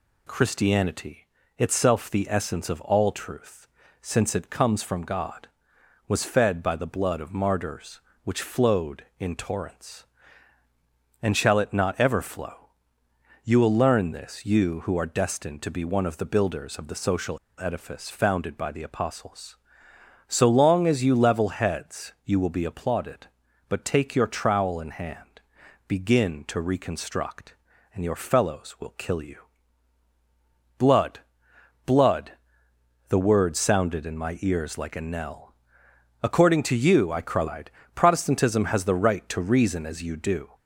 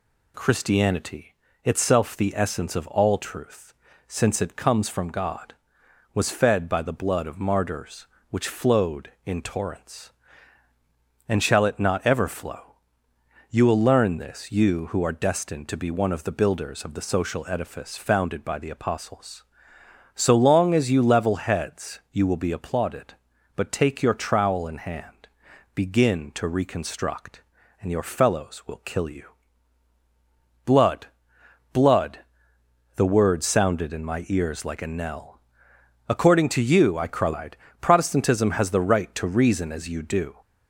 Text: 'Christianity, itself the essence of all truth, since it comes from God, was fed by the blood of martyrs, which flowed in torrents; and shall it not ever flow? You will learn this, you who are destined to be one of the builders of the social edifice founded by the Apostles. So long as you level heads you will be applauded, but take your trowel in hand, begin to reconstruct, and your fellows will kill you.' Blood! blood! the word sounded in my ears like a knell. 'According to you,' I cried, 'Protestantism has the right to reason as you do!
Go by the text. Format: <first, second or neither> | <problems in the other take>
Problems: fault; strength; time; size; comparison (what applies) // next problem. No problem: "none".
second | pauses between "social" and "edifice"; slight; at 17.3 s; 0.22 s long